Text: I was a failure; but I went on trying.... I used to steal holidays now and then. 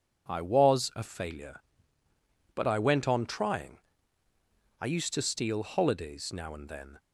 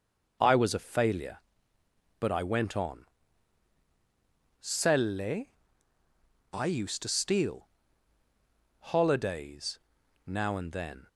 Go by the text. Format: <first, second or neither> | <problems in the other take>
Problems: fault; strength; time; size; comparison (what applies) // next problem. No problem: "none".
first | says "selle" for "trying"; at 4.5 s // pauses between "steal" and "holidays"; at 7.6 s; 1.1 s long // pauses between "holidays" and "now"; noticeable; at 9.7 s; 0.46 s long